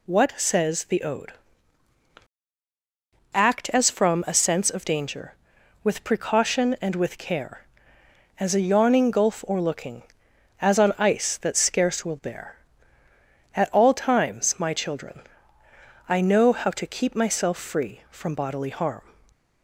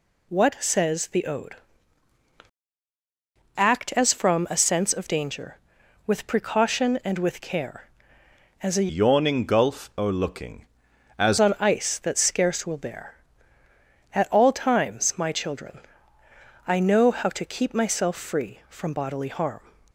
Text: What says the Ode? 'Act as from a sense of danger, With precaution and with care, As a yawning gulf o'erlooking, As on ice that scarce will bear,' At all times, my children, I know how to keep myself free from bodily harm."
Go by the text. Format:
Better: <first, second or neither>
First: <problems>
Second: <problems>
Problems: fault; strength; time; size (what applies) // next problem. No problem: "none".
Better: first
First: none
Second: changes voice from "yawning" to "As"; from 8.8 to 11.3 s; 2.5 s long